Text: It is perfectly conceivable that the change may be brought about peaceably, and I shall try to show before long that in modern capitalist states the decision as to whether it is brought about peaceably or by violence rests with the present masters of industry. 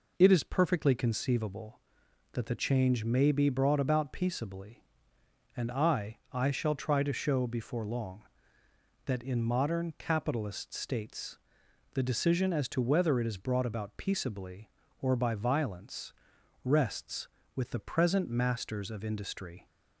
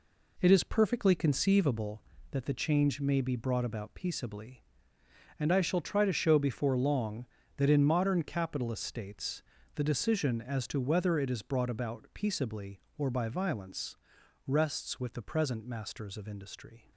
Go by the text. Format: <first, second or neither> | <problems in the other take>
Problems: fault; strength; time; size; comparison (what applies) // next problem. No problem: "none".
second | says "I" twice; at 6.3 s // pauses between "states" and "the"; noticeable; at 11.3 s; 0.56 s long; slight in the second // pauses between "violence" and "rests"; noticeable; at 16.1 s; 0.52 s long; noticeable in the second